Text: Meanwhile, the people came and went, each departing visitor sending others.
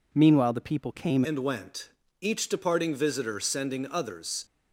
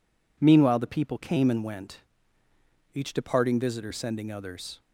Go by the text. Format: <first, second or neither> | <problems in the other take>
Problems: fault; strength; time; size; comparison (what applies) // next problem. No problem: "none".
second | changes voice at "and"; from 1.2 s on; 3.2 s long